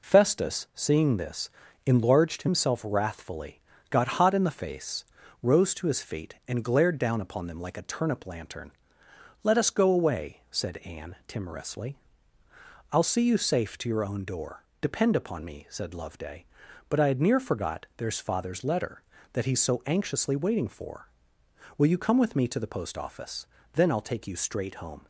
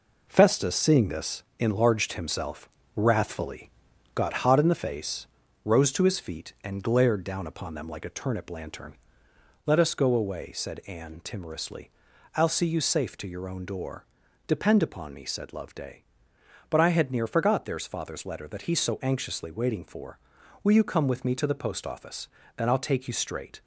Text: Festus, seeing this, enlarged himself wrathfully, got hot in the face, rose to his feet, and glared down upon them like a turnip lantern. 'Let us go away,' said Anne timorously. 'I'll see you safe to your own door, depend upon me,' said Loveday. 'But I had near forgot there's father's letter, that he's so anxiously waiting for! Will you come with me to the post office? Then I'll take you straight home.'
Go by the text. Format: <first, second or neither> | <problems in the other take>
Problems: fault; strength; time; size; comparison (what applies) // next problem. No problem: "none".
first | pauses between "himself" and "wrathfully"; slight; at 2.6 s; 0.26 s long // stops before "home"; at 23.6 s